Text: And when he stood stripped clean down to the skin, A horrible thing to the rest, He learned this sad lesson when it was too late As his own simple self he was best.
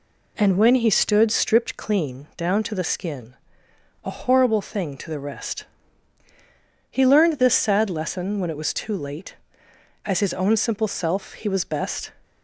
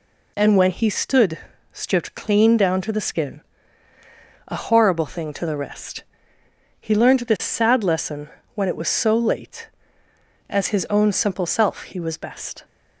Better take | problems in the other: first | pauses between "stood" and "stripped"; slight; at 1.3 s; 0.34 s long // pauses between "lesson" and "when"; slight; at 8.2 s; 0.24 s long // says "so" for "too"; at 8.8 s

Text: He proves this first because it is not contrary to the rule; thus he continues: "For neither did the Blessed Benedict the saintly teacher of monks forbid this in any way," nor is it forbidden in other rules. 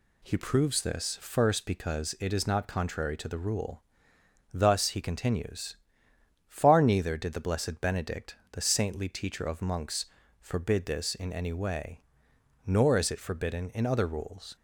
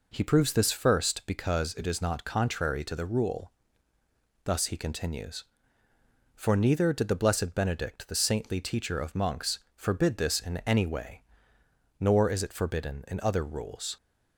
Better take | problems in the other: second | says "Far" for "For"; at 6.4 s // pauses between "monks" and "forbid"; slight; at 10.0 s; 0.34 s long

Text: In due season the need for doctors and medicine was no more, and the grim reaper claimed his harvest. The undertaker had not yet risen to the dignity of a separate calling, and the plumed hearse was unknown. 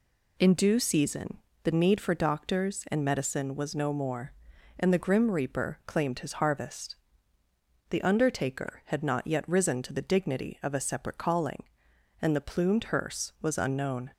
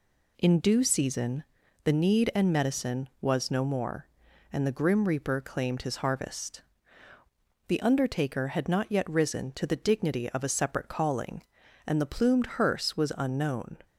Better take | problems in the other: first | pauses between "season" and "the"; at 1.4 s; 0.40 s long; slight in the first // skips "for doctors"; at 2.3 s

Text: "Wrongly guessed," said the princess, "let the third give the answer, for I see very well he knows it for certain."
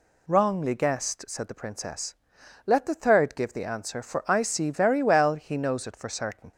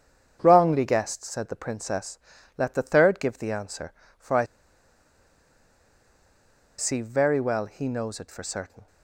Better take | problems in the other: first | starts louder than the rest; strong; until 1.4 s; 8 dB // pauses between "I" and "see"; strong; at 4.4 s; 2.3 s long

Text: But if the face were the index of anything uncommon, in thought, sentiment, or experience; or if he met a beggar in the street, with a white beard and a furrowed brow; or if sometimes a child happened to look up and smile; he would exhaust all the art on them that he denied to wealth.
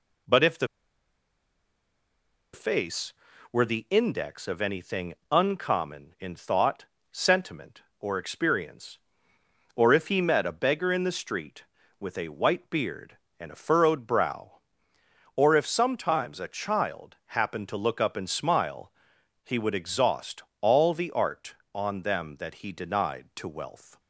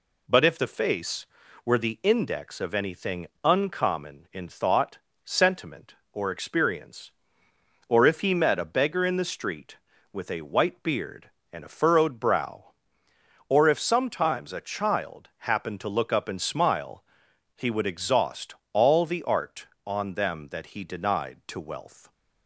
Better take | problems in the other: second | pauses between "the" and "face"; strong; at 0.6 s; 1.8 s long // pauses between "anything" and "uncommon"; slight; at 5.1 s; 0.16 s long; slight in the second // pauses between "exhaust" and "all"; slight; at 20.4 s; 0.20 s long; slight in the second

